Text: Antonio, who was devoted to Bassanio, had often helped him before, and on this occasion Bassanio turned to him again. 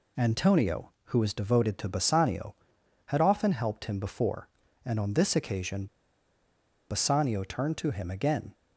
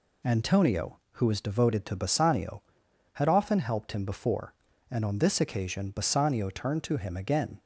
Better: second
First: pauses between "occasion" and "Bassanio"; at 5.8 s; 1.0 s long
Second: none

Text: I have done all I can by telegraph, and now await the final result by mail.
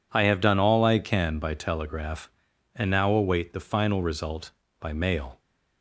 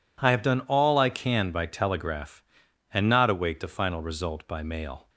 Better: first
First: none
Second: says "not" for "now"; at 3.0 s

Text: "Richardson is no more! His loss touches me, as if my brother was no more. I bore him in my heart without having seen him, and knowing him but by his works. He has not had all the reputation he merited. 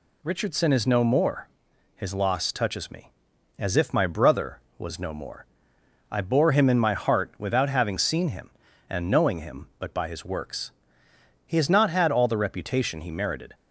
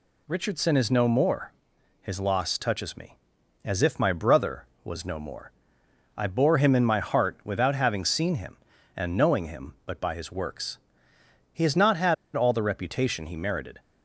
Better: first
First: none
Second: pauses between "had" and "all"; slight; at 12.1 s; 0.21 s long

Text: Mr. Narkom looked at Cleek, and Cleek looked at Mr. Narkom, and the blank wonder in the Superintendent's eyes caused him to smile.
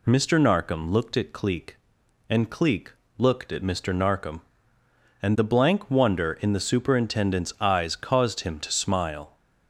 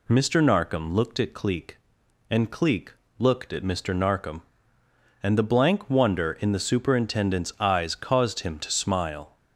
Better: neither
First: pauses between "Cleek" and "looked"; slight; at 2.9 s; 0.26 s long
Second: pauses between "Cleek" and "looked"; slight; at 2.9 s; 0.26 s long

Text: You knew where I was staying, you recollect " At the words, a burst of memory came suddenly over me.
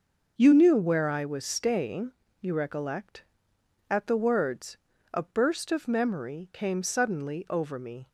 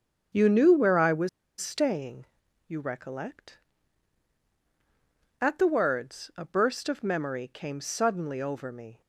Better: first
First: none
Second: starts louder than the rest; until 1.6 s; 6.5 dB // pauses between "was" and "staying"; slight; at 1.2 s; 0.29 s long

